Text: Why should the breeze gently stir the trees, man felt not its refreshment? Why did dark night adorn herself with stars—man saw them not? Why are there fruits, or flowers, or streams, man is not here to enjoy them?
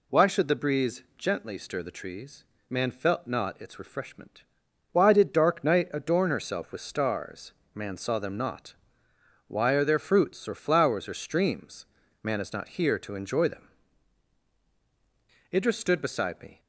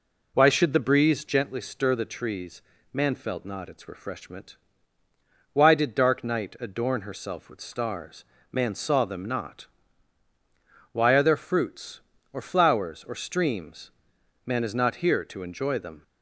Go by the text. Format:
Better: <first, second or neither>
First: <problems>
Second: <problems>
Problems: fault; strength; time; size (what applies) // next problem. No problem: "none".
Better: second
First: goes on to say "Idris stood beside me"; noticeable; from 15.5 s on; 1.0 s long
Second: none